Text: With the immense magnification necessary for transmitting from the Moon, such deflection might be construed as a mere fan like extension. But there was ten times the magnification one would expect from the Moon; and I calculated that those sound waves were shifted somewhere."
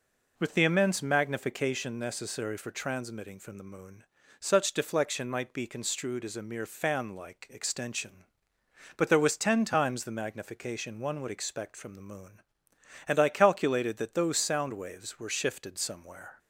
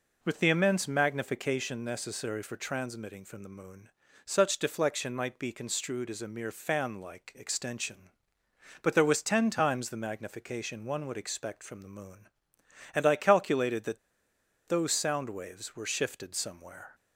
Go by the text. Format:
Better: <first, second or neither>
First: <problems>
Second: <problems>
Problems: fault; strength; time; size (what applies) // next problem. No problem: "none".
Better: first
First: none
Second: pauses between "that" and "those"; noticeable; at 13.9 s; 0.69 s long